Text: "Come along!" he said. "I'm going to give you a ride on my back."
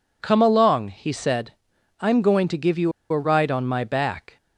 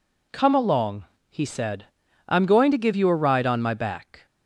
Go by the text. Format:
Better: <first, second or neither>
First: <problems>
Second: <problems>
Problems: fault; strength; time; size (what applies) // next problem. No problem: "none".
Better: second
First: pauses between "you" and "a"; slight; at 2.9 s; 0.19 s long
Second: none